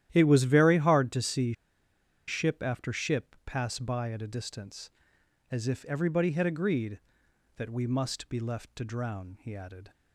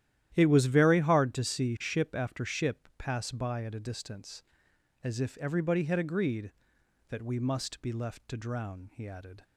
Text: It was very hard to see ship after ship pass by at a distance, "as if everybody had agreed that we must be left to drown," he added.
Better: second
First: starts louder than the rest; strong; until 1.1 s; 12 dB // pauses between "see" and "ship"; noticeable; at 1.5 s; 0.74 s long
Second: starts louder than the rest; strong; until 1.3 s; 12 dB

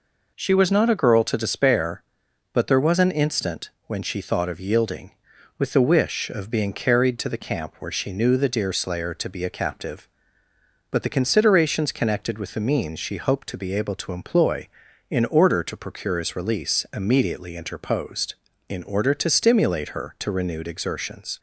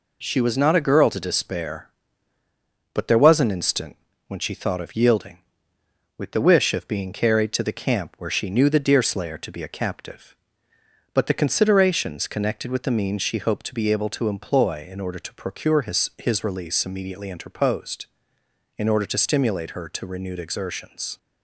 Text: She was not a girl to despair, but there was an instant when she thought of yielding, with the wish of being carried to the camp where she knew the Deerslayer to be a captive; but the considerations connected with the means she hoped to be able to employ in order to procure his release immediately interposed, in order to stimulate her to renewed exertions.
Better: first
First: pauses between "instant" and "when"; slight; at 3.7 s; 0.16 s long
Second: pauses between "instant" and "when"; slight; at 3.9 s; 0.32 s long // says "his" twice; at 16.1 s

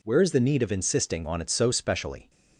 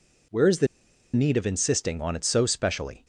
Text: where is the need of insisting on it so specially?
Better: first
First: none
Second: pauses between "the" and "need"; noticeable; at 0.6 s; 0.47 s long

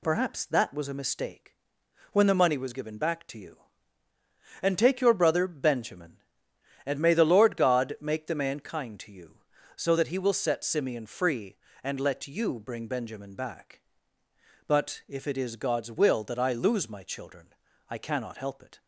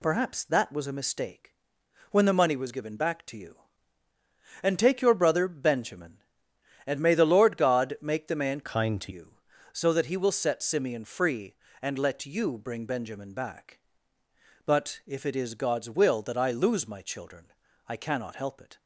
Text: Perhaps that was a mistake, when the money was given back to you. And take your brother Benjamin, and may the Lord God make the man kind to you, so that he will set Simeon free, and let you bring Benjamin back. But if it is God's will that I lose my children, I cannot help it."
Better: first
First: none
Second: changes voice from "kind" to "to"; from 8.6 to 9.1 s; 0.5 s long

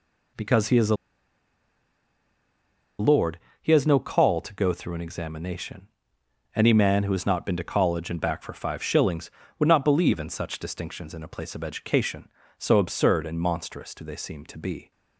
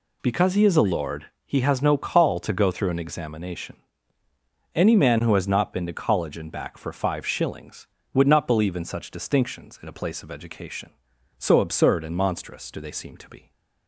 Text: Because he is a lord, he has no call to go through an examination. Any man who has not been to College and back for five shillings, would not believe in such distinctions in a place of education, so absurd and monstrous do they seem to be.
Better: second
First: pauses between "a" and "lord"; strong; at 0.9 s; 2.0 s long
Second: none

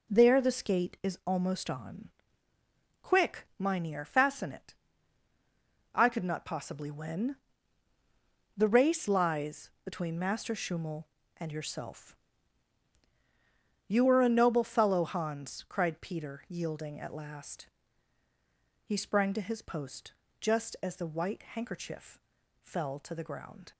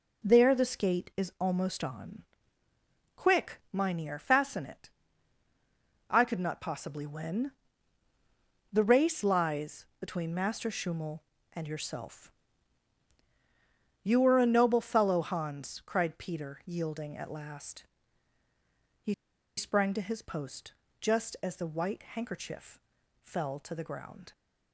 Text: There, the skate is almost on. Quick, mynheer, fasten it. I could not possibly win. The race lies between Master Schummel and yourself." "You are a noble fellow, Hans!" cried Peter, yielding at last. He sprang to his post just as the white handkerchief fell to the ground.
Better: first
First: pauses between "post" and "just"; slight; at 20.1 s; 0.26 s long // pauses between "handkerchief" and "fell"; at 22.1 s; 0.42 s long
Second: pauses between "He" and "sprang"; at 19.1 s; 0.44 s long // pauses between "post" and "just"; slight; at 20.7 s; 0.26 s long // pauses between "handkerchief" and "fell"; at 22.7 s; 0.42 s long

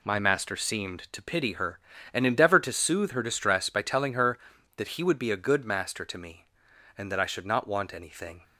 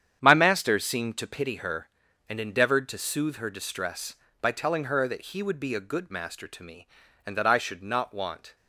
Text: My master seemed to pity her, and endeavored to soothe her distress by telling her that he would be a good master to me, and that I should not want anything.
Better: first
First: none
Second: starts louder than the rest; strong; until 1.2 s; 9 dB // stops before "anything"; at 8.5 s

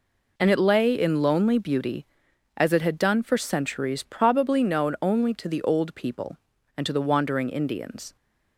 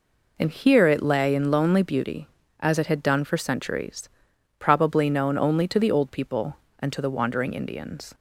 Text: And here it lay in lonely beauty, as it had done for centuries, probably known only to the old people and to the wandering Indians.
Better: second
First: skips "here"; at 0.4 s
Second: none

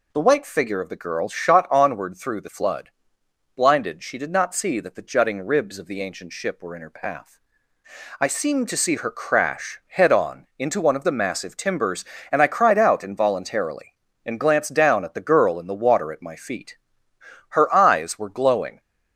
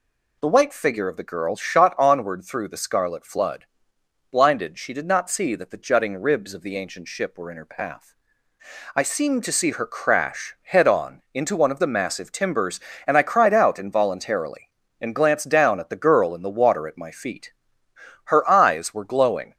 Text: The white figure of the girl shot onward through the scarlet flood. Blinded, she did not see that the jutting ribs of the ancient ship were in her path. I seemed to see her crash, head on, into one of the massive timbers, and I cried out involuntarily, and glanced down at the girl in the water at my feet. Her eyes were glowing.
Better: second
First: skips "scarlet"; at 2.4 s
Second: none

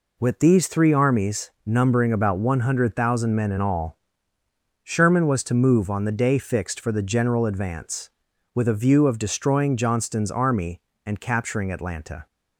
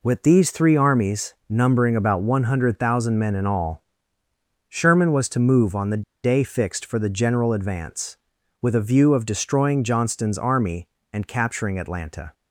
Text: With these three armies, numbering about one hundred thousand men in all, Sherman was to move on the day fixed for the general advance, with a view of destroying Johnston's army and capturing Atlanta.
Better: first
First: none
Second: pauses between "the" and "day"; slight; at 6.0 s; 0.20 s long

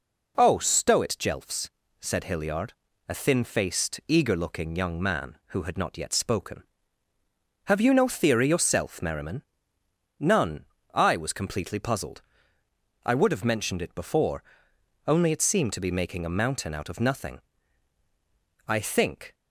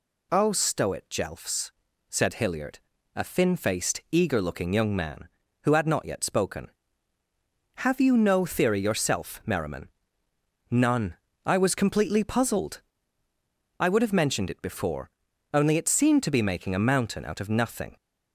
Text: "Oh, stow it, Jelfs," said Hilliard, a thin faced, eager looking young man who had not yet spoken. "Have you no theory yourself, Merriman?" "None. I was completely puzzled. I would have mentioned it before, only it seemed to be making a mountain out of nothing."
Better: second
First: goes on to say "I think"; noticeable; from 18.6 s on; 0.66 s long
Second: none

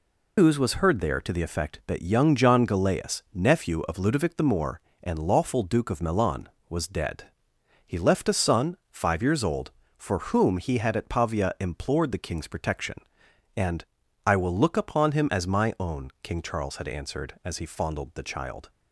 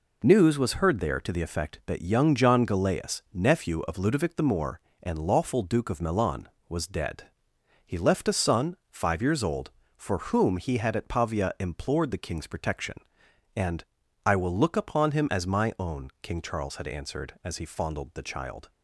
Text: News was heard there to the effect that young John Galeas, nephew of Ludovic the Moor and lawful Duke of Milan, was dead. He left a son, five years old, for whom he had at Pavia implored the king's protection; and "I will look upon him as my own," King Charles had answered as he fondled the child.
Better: second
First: loses the start of "News"; at 0.3 s; 145 ms // pauses between "and" and "I"; at 13.8 s; 0.40 s long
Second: pauses between "and" and "I"; at 13.8 s; 0.40 s long

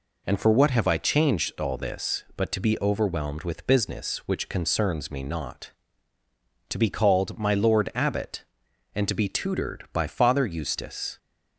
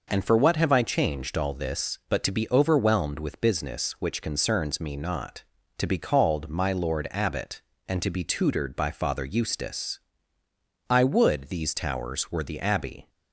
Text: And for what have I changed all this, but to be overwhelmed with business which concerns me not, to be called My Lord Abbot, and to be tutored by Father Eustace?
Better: first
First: none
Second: goes on to say "I would these towers were the Abbey"; strong; from 10.8 s on; 2.2 s long

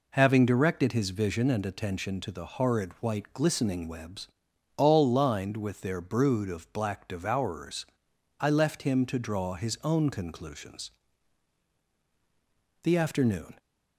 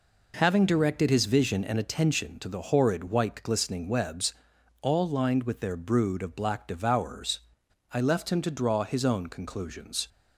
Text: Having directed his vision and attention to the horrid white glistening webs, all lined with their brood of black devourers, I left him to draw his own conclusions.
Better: second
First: goes on to say "The afternoon"; noticeable; from 12.8 s on; 0.74 s long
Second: none

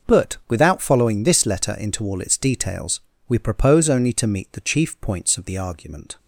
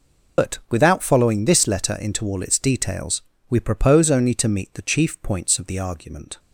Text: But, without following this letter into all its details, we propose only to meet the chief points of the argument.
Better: first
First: none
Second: loses the start of "But"; at 0.3 s; 115 ms

